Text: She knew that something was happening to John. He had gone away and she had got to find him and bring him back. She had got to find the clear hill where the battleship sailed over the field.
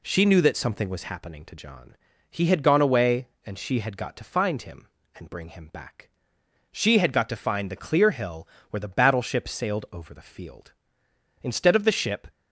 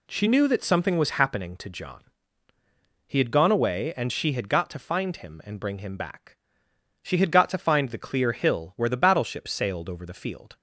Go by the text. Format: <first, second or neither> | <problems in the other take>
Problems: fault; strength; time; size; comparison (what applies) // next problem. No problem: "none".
second | pauses between "hill" and "where"; slight; at 8.4 s; 0.24 s long // goes on to say "Instead of the ship"; noticeable; from 11.4 s on; 0.86 s long